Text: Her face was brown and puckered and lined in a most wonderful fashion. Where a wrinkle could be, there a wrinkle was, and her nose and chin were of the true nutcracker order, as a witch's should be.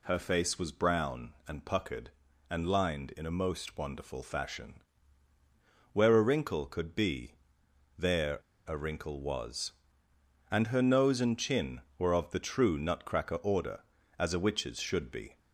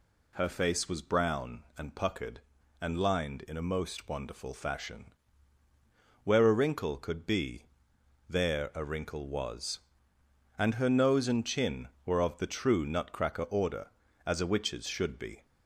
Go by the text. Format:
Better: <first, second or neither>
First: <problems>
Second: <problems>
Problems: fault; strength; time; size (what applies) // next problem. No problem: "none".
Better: second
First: pauses between "there" and "a"; slight; at 8.3 s; 0.29 s long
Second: none